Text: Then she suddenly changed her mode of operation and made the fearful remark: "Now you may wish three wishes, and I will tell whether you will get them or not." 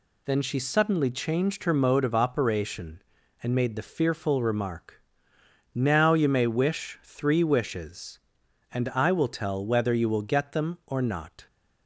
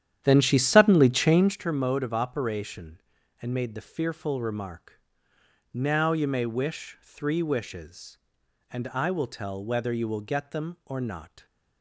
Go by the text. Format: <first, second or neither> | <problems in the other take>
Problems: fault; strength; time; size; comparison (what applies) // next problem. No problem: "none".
first | starts louder than the rest; strong; until 1.6 s; 10.5 dB